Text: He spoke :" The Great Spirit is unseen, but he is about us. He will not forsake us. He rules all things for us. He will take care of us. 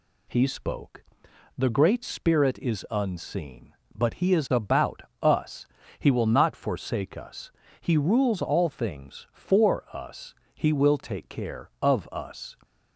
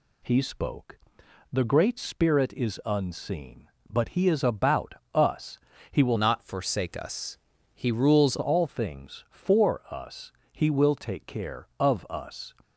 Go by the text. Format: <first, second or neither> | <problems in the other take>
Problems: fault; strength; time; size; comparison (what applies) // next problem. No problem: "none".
first | pauses between "about" and "us"; slight; at 4.9 s; 0.20 s long; slight in the first // changes voice from "not" to "rules"; from 6.1 to 8.3 s; 2.2 s long